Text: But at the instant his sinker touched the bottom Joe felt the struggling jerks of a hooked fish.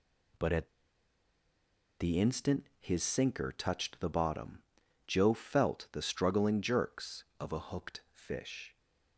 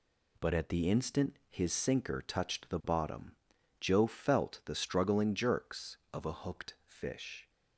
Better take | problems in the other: second | pauses between "at" and "the"; strong; at 0.6 s; 1.3 s long // pauses between "bottom" and "Joe"; noticeable; at 4.6 s; 0.46 s long; noticeable in the second

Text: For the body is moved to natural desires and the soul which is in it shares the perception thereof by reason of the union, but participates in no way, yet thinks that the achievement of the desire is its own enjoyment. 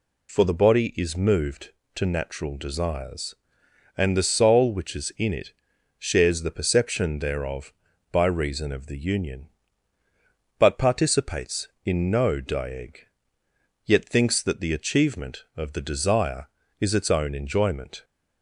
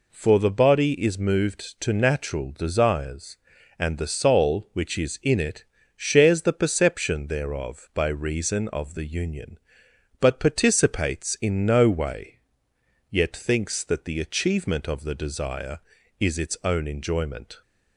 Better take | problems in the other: second | pauses between "it" and "shares"; at 5.5 s; 0.44 s long; slight in the second // says "dieg" for "way"; at 12.3 s

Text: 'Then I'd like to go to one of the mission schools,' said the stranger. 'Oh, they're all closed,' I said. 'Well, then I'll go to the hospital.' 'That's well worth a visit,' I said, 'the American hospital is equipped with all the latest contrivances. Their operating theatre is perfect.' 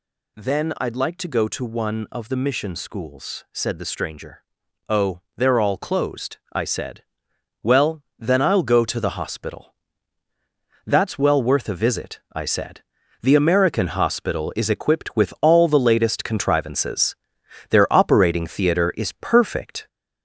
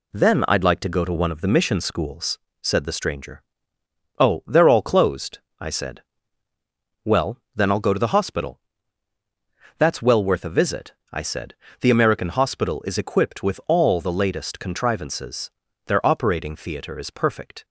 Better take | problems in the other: second | gets louder; noticeable; throughout; 5 dB

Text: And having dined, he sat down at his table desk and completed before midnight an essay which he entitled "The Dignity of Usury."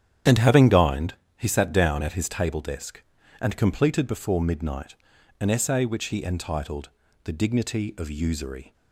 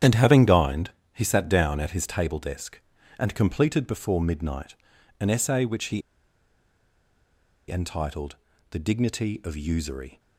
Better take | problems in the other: first | starts louder than the rest; strong; until 1.2 s; 9.5 dB; strong in the first // pauses between "midnight" and "an"; noticeable; at 4.7 s; 0.46 s long; noticeable in the first // pauses between "he" and "entitled"; strong; at 6.0 s; 1.6 s long // pauses between "entitled" and "The"; slight; at 8.3 s; 0.36 s long; slight in the first

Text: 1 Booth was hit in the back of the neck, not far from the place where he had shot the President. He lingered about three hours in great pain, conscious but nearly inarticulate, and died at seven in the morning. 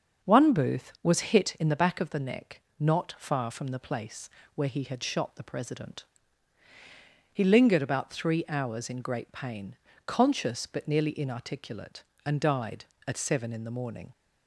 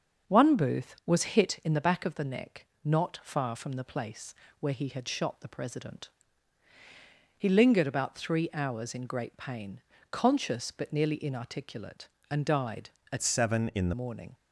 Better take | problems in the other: first | starts louder than the rest; until 1.3 s; 6.5 dB; noticeable in the first // pauses between "place" and "where"; slight; at 4.3 s; 0.26 s long; slight in the first // changes voice from "seven" to "the"; from 13.2 to 13.9 s; 0.7 s long

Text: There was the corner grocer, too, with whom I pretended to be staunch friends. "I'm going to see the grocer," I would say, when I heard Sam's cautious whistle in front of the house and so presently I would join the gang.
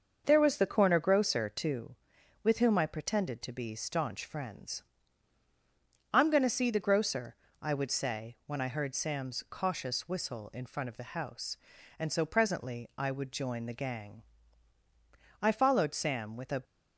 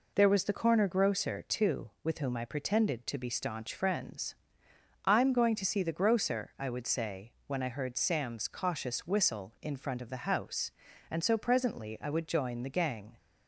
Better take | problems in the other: second | starts louder than the rest; until 1.2 s; 6.5 dB // goes on to say "I followed Sam with a"; noticeable; from 15.4 s on; 1.2 s long

